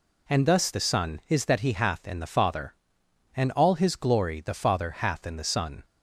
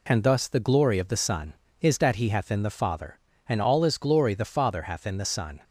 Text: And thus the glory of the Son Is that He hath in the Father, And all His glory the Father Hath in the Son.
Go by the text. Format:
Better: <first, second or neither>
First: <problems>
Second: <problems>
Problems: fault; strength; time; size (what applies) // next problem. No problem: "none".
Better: second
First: skips "the glory of"; at 0.7 s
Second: none